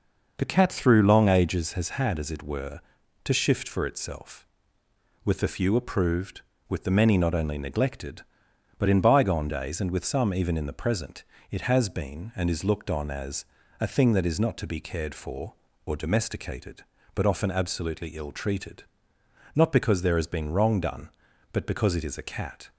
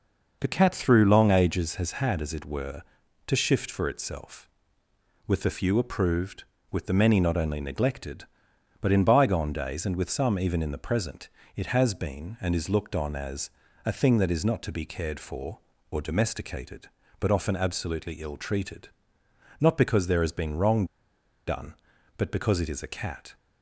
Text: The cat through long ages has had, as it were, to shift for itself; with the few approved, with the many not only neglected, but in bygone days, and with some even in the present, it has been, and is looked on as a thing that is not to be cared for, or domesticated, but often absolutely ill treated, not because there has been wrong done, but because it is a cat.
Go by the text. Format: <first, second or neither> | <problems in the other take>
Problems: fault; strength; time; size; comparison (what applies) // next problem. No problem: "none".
first | pauses between "as" and "a"; slight; at 13.4 s; 0.34 s long; slight in the first // pauses between "wrong" and "done"; noticeable; at 20.8 s; 0.61 s long